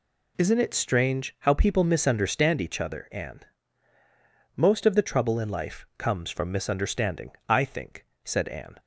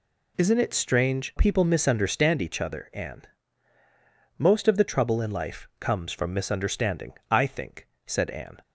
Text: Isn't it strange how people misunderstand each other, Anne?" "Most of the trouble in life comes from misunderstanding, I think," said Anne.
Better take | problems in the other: first | skips "how"; at 1.3 s

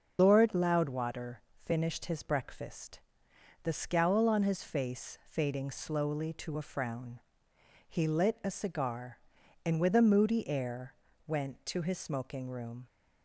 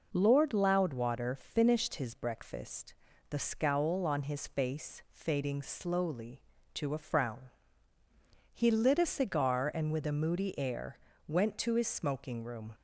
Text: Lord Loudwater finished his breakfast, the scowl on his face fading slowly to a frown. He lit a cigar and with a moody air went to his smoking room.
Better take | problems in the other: second | loses the start of "Lord"; at 0.1 s; 70 ms // starts louder than the rest; until 1.1 s; 6.5 dB // pauses between "Loudwater" and "finished"; slight; at 1.4 s; 0.24 s long // pauses between "air" and "went"; slight; at 10.9 s; 0.32 s long; slight in the second

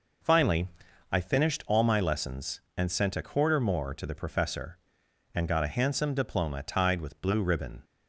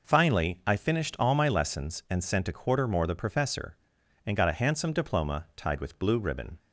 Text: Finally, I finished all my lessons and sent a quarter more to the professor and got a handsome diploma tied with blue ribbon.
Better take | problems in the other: first | skips "to"; at 3.0 s

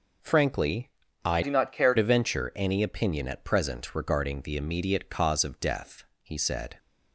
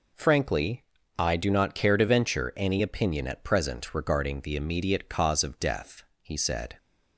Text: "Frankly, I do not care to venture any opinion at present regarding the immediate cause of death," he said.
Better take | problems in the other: second | changes voice from "do" to "care"; from 1.4 to 1.9 s; 0.5 s long

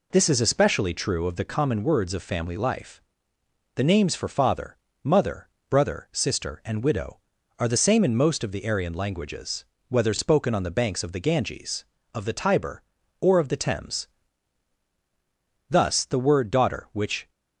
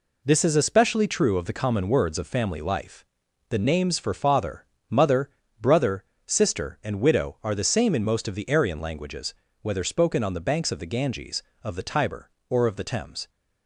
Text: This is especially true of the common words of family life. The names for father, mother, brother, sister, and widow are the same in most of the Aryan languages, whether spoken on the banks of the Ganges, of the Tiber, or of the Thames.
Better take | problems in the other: second | goes on to say "Thus the word daughter which"; from 15.6 s on; 1.6 s long

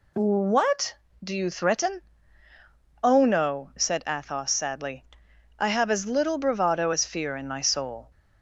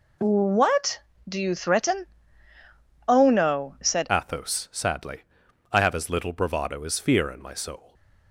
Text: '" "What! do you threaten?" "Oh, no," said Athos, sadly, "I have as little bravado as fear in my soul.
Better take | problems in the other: first | changes voice at "Athos"; from 4.1 s on; 3.8 s long

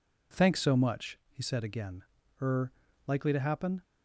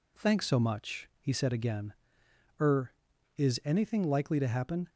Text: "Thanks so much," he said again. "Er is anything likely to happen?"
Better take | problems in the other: second | skips "is anything"; at 2.8 s

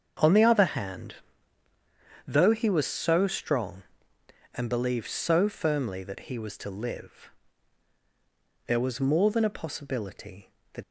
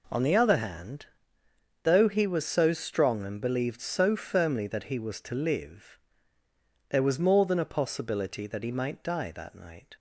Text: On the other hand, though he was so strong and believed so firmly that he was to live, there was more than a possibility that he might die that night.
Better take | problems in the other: second | starts louder than the rest; until 2.3 s; 7 dB // stops before "he might die that night"; at 10.8 s

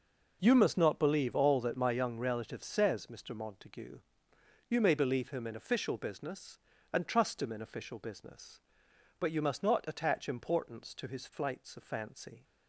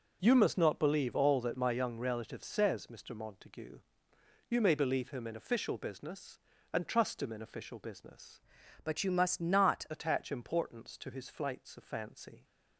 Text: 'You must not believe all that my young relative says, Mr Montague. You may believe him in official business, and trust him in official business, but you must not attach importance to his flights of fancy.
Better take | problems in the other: first | changes voice from "but" to "not"; from 8.8 to 9.8 s; 1.0 s long

